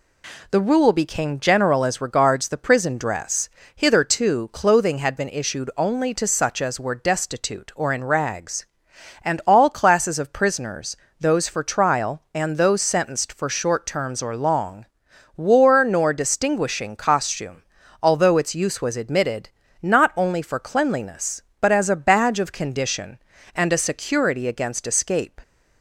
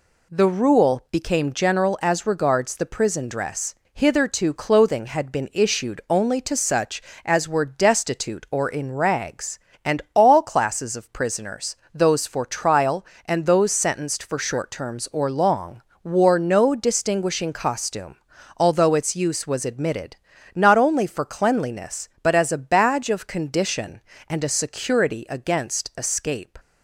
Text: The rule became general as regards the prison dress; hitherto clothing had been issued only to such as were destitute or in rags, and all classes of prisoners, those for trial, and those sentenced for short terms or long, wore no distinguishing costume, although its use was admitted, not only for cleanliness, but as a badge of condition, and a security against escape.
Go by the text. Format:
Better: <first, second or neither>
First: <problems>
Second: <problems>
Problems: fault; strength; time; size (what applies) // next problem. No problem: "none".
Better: second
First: says "nor" for "no"; at 15.8 s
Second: none